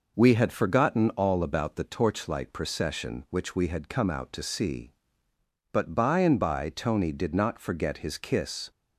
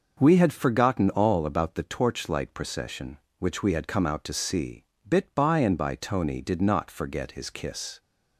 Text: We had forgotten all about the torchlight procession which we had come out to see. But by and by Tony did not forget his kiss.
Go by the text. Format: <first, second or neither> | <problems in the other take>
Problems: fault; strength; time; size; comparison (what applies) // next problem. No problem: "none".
first | says "Bit" for "But"; at 5.0 s